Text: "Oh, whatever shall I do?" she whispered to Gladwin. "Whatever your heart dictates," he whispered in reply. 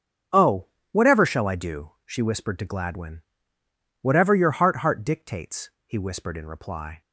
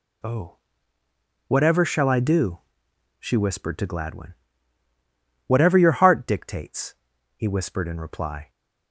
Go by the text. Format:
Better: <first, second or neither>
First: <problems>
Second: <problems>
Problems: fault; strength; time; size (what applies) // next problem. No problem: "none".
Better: second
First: starts louder than the rest; strong; until 1.5 s; 8 dB // says "heart" twice; at 4.7 s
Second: none